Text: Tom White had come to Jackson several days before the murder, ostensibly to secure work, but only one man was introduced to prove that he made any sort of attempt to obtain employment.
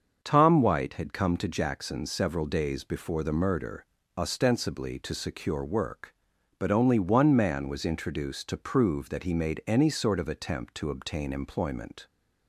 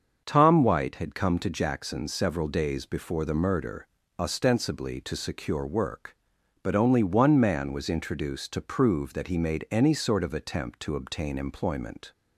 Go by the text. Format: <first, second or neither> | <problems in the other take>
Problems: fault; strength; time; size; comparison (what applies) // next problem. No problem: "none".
neither | starts louder than the rest; the same in both